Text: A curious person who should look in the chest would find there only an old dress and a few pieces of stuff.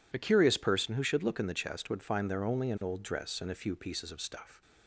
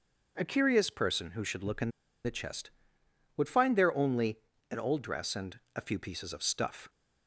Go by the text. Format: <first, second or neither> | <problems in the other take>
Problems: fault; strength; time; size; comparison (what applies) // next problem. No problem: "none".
first | pauses between "in" and "the"; at 1.8 s; 0.36 s long // pauses between "only" and "an"; slight; at 4.3 s; 0.32 s long // pauses between "and" and "a"; slight; at 5.5 s; 0.16 s long